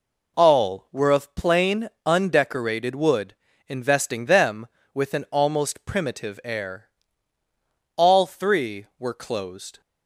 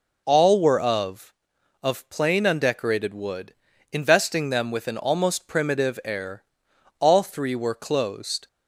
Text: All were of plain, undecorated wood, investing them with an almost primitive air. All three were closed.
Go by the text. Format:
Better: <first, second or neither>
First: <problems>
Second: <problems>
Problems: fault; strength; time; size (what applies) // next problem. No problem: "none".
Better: first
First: none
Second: says "of" twice; at 1.8 s